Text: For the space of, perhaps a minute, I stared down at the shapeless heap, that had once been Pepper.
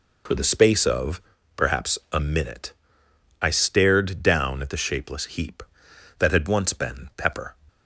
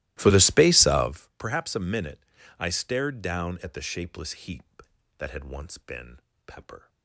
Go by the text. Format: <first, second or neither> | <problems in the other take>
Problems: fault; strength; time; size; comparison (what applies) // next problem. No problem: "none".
first | starts louder than the rest; strong; until 1.2 s; 17.5 dB // pauses between "been" and "Pepper"; slight; at 6.1 s; 0.30 s long